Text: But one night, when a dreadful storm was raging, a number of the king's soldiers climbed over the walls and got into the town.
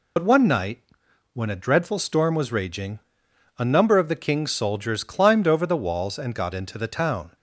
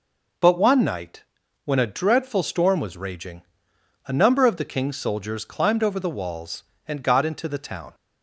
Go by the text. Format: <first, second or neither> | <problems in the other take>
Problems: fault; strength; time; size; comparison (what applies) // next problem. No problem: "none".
second | loses the start of "But"; at 0.1 s; 70 ms